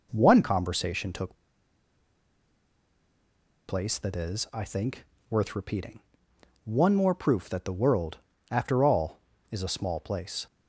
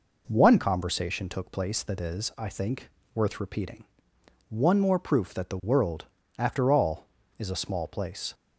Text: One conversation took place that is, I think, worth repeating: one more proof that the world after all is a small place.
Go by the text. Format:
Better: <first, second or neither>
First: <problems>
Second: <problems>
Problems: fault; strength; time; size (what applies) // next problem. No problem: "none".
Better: second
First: pauses between "took" and "place"; strong; at 1.3 s; 2.3 s long // pauses between "world" and "after"; slight; at 8.1 s; 0.34 s long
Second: pauses between "world" and "after"; slight; at 6.0 s; 0.34 s long